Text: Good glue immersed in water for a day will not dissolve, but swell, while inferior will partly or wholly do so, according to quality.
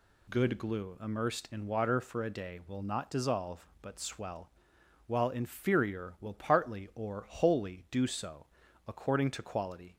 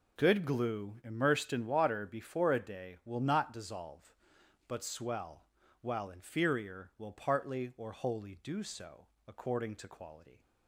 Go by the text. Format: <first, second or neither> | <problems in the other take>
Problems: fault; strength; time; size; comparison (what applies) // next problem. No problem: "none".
first | says "before" for "for"; at 2.0 s